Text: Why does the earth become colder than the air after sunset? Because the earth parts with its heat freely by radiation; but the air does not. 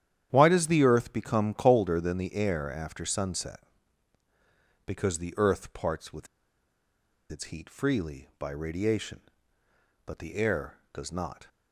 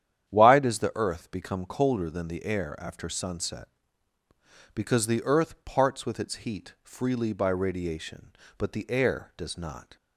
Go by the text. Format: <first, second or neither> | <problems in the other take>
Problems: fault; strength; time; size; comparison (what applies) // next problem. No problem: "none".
second | starts louder than the rest; strong; until 1.3 s; 10 dB; strong in the second // pauses between "with" and "its"; at 6.2 s; 1.0 s long